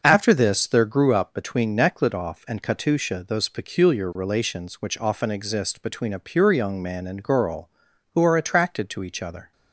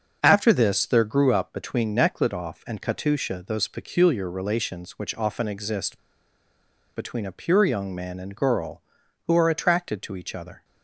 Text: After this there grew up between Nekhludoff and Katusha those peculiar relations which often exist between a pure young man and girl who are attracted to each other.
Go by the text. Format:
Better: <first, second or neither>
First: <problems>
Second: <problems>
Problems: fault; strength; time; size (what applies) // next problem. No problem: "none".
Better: first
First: starts louder than the rest; until 1.0 s; 6.5 dB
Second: starts louder than the rest; until 1.2 s; 6.5 dB // pauses between "exist" and "between"; noticeable; at 5.9 s; 0.95 s long